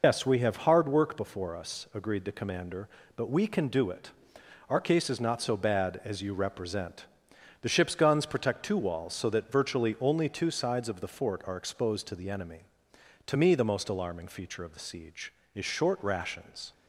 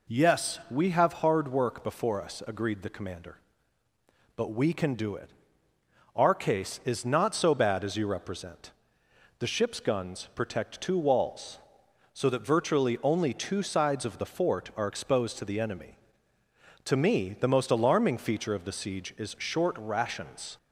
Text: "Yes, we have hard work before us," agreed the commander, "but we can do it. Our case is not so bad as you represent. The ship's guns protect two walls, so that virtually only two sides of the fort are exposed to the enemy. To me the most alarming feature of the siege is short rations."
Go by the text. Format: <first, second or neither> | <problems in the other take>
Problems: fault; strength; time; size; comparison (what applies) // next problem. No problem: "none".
second | loses the start of "Yes"; at 0.0 s; 95 ms